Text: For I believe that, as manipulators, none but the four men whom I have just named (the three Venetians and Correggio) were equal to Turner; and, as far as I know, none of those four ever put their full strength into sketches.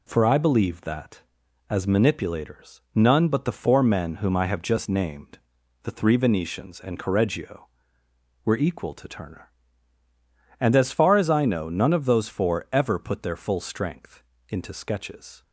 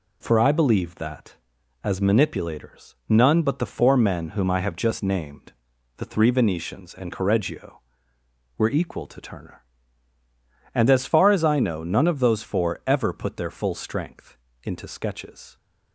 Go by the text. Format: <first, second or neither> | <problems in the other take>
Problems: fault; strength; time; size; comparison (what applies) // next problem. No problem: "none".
neither | pauses between "strength" and "into"; slight; the same in both